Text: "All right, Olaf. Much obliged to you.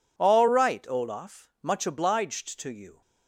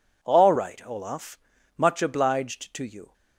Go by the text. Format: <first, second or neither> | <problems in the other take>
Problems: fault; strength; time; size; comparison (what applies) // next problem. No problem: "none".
neither | none